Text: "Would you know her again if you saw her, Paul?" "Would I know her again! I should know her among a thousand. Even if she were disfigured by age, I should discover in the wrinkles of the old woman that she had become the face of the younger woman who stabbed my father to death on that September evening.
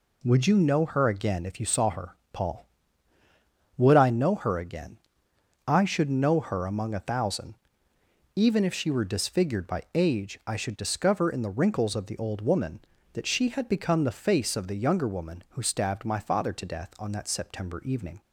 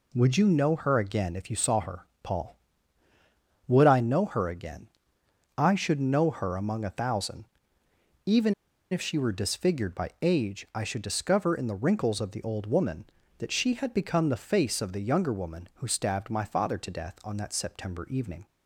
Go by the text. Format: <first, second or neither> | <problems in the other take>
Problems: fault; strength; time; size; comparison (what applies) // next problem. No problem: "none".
first | pauses between "Even" and "if"; at 8.5 s; 0.37 s long